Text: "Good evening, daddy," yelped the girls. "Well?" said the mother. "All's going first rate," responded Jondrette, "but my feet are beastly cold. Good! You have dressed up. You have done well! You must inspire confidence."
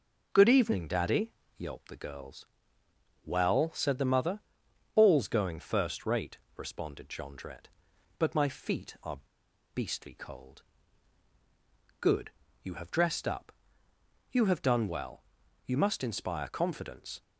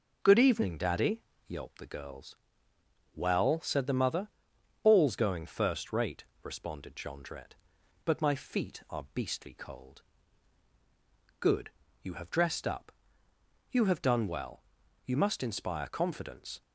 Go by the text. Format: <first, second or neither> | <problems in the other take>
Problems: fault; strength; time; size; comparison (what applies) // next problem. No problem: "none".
second | pauses between "are" and "beastly"; noticeable; at 9.1 s; 0.55 s long